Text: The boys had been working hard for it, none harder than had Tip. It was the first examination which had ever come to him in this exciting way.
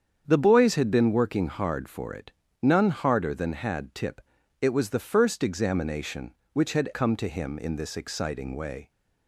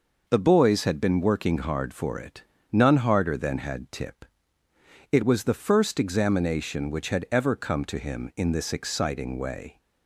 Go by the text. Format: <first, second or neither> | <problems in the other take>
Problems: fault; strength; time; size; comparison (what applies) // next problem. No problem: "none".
second | starts louder than the rest; strong; until 1.2 s; 8 dB // skips "ever"; at 6.9 s